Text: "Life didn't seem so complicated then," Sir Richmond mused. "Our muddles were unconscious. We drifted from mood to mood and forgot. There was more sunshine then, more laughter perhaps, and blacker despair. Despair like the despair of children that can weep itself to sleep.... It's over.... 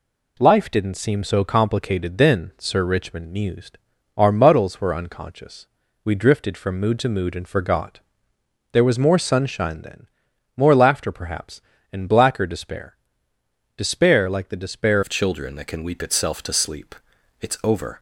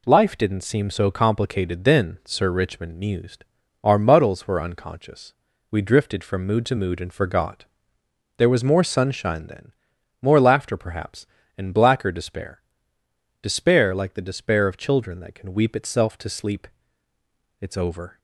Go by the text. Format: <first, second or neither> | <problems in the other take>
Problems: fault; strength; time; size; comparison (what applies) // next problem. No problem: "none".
second | changes voice at "of"; from 15.0 s on; 2.9 s long